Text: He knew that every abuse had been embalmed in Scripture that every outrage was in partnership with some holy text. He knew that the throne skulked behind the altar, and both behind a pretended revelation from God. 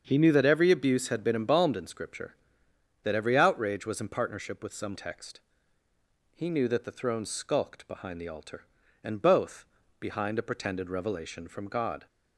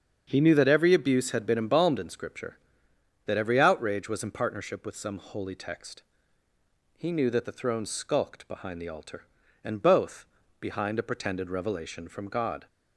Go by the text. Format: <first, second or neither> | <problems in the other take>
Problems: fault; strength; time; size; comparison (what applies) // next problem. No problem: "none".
second | starts louder than the rest; until 1.0 s; 7 dB; strong in the second // skips "holy"; at 4.9 s // pauses between "both" and "behind"; slight; at 9.6 s; 0.34 s long; slight in the second